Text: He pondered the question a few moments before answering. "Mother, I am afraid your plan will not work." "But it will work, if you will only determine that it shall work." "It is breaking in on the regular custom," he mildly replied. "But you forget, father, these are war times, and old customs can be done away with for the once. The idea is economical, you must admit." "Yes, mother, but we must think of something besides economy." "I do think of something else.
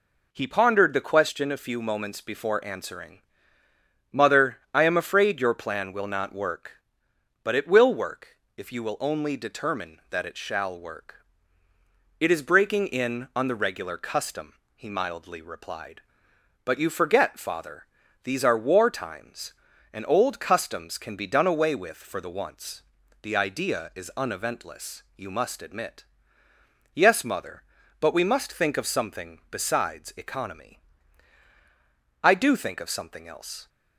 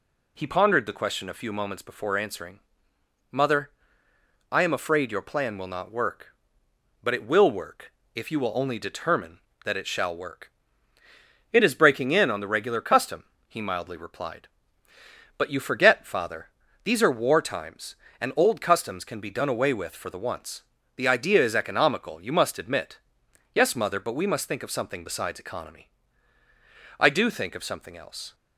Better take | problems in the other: second | says "uneventless" for "economical"; at 24.1 s

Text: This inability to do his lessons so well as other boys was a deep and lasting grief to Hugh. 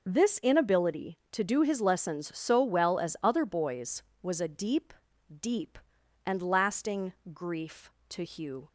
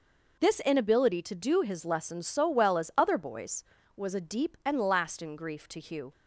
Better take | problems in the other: second | says "deep" twice; at 5.3 s // pauses between "lasting" and "grief"; slight; at 7.1 s; 0.20 s long

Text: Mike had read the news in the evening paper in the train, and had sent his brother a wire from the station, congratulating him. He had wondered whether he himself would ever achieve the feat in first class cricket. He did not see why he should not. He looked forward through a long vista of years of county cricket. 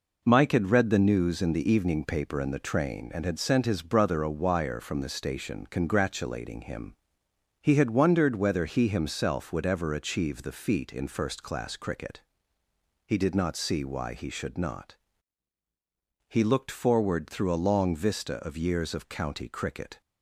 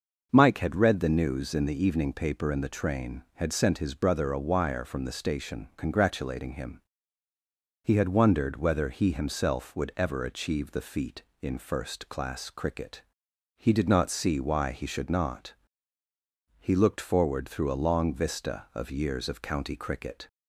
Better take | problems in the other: first | skips "and"; at 3.2 s

